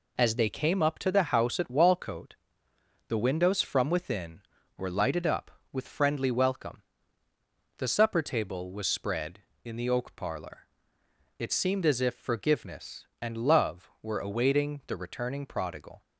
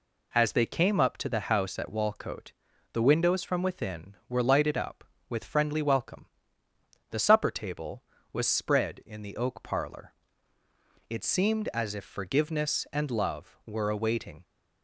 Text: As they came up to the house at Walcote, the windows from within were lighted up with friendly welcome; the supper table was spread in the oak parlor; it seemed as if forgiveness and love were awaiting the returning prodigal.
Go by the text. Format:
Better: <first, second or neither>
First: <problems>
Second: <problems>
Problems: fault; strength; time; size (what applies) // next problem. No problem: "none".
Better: first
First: none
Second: stops before "the returning prodigal"; at 14.4 s